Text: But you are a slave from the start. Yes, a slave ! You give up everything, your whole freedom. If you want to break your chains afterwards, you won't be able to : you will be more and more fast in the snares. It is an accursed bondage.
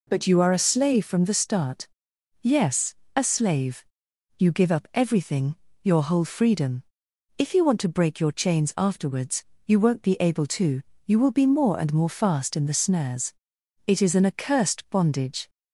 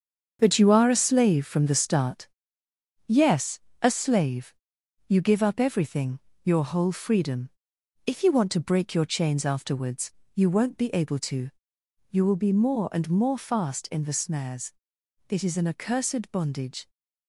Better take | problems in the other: first | gets quieter; strong; throughout; 9 dB

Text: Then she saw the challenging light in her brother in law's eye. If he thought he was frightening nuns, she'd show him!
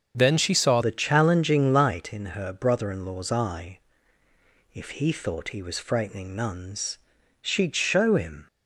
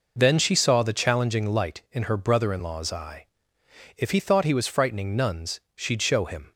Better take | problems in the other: second | starts louder than the rest; until 1.1 s; 7 dB // changes voice at "the"; from 0.8 s on; 7.6 s long

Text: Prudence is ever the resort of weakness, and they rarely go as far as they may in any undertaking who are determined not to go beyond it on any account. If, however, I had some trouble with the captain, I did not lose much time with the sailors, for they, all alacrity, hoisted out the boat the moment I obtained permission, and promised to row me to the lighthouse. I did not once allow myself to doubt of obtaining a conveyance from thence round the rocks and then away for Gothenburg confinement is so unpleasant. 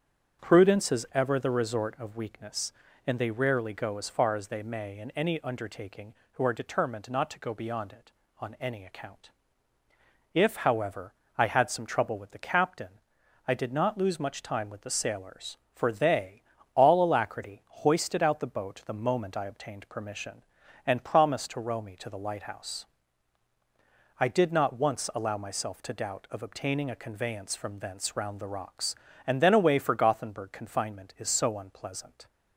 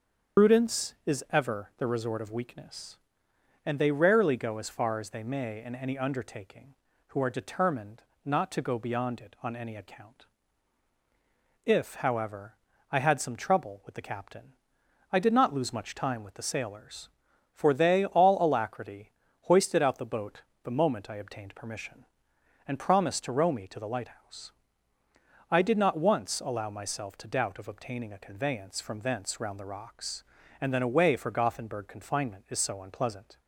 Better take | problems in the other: first | loses the start of "Prudence"; at 0.3 s; 115 ms // starts louder than the rest; strong; until 1.5 s; 7 dB; strong in the first // pauses between "determined" and "not"; slight; at 8.0 s; 0.22 s long // pauses between "boat" and "the"; slight; at 20.4 s; 0.20 s long

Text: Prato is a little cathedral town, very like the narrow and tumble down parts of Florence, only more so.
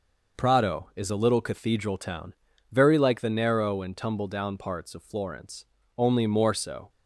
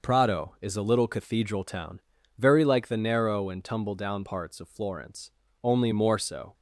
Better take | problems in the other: neither | none

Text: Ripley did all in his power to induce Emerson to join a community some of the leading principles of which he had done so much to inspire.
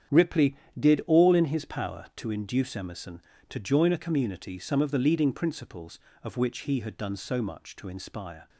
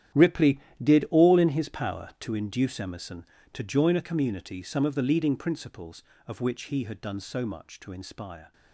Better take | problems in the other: first | gets quieter; strong; throughout; 15 dB // starts louder than the rest; strong; until 1.4 s; 11.5 dB; strong in the first

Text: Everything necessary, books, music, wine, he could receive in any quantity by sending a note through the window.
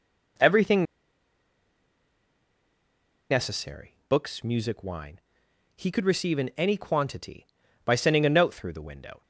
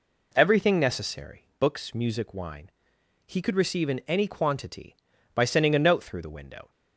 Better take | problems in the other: second | pauses between "Everything" and "necessary"; strong; at 0.8 s; 2.4 s long

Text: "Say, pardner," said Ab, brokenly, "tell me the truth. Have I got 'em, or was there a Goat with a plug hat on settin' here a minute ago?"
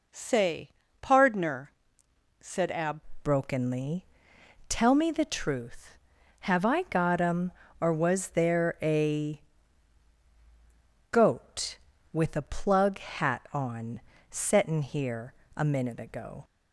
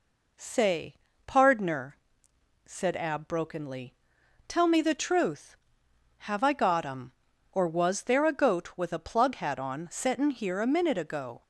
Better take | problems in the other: second | changes voice at "brokenly"; from 3.2 s on; 13.2 s long // pauses between "a" and "Goat"; strong; at 9.4 s; 1.6 s long // pauses between "on" and "settin"; slight; at 13.9 s; 0.30 s long // pauses between "here" and "a"; slight; at 15.3 s; 0.22 s long

